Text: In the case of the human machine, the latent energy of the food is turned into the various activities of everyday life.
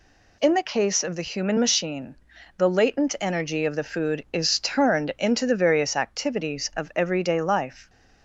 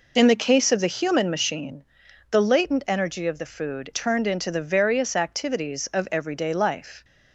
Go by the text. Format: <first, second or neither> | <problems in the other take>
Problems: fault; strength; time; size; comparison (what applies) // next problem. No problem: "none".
first | skips "is"; at 3.9 s